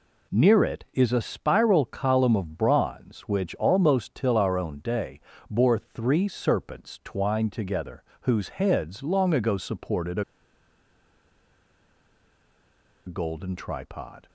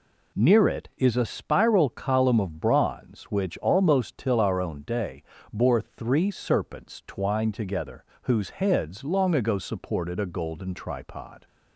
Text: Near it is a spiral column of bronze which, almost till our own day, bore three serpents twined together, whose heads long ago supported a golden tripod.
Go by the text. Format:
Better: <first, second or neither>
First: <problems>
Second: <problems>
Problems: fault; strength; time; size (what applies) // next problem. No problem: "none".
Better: second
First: pauses between "a" and "golden"; strong; at 10.2 s; 2.8 s long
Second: none